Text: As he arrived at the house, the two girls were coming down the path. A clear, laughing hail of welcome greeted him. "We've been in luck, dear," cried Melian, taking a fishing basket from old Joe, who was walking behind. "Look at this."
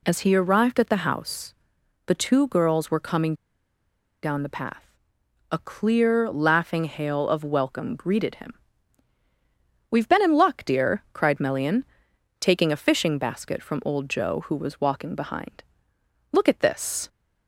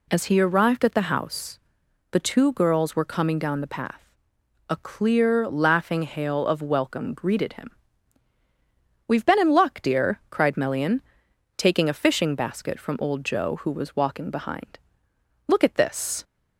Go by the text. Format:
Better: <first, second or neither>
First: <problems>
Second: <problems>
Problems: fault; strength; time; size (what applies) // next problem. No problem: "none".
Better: second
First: pauses between "coming" and "down"; noticeable; at 3.3 s; 0.90 s long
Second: none